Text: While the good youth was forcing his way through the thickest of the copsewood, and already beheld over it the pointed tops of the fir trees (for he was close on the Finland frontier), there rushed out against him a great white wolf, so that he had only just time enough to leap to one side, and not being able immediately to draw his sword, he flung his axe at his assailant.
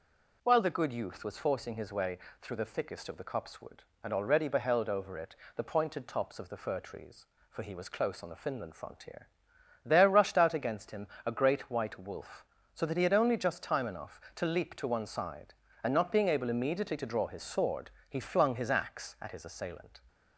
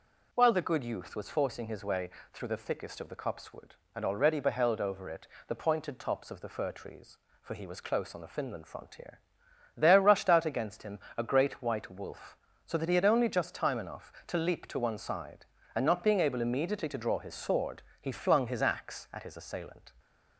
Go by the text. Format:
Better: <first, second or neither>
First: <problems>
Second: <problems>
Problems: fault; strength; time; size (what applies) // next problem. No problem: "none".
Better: neither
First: pauses between "way" and "through"; slight; at 2.1 s; 0.22 s long // pauses between "it" and "the"; slight; at 5.3 s; 0.22 s long // pauses between "him" and "a"; slight; at 11.0 s; 0.18 s long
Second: pauses between "way" and "through"; slight; at 2.0 s; 0.22 s long // pauses between "it" and "the"; slight; at 5.2 s; 0.22 s long // pauses between "him" and "a"; slight; at 10.9 s; 0.18 s long